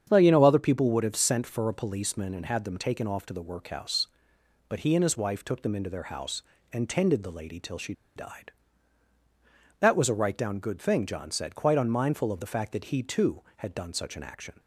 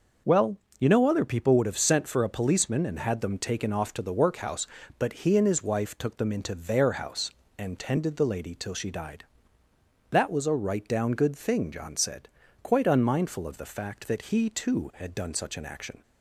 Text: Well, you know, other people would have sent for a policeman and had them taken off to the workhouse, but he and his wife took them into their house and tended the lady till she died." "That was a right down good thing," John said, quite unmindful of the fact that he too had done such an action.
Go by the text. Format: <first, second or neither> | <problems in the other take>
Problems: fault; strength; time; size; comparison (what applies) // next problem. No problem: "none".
second | starts louder than the rest; strong; until 1.1 s; 8 dB // pauses between "she" and "died"; slight; at 7.9 s; 0.23 s long